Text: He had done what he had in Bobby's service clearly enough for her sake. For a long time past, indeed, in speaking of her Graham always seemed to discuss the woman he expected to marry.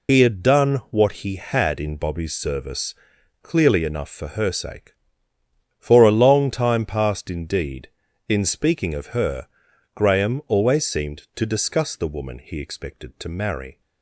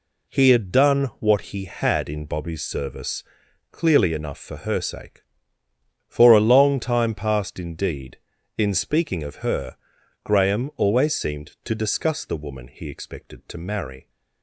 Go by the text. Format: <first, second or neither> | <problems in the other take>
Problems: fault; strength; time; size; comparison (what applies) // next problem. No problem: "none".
second | loses the start of "He"; at 0.0 s; 90 ms // pauses between "service" and "clearly"; noticeable; at 2.9 s; 0.48 s long; noticeable in the second // pauses between "her" and "Graham"; noticeable; at 9.4 s; 0.50 s long; noticeable in the second